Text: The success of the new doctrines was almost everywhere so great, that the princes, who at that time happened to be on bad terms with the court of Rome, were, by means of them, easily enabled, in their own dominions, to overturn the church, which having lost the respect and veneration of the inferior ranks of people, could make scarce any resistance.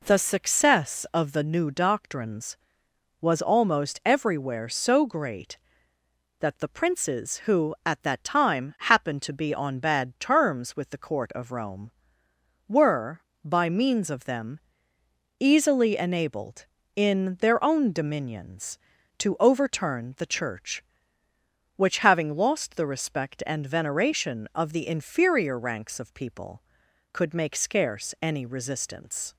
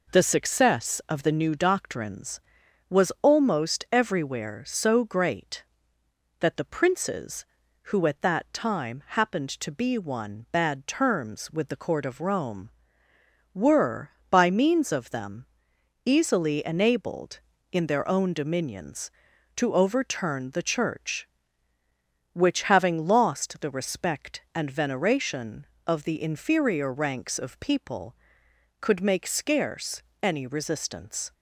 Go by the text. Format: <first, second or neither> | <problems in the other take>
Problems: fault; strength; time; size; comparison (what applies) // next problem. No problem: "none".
first | says "one" for "on"; at 9.9 s // pauses between "scarce" and "any"; slight; at 30.0 s; 0.20 s long